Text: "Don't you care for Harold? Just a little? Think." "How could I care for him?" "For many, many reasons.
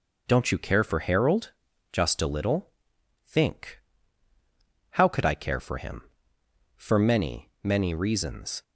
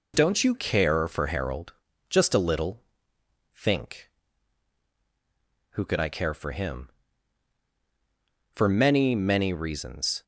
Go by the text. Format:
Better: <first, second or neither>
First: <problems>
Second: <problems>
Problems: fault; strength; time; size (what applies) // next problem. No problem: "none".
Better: first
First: none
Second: says "Who" for "How"; at 5.7 s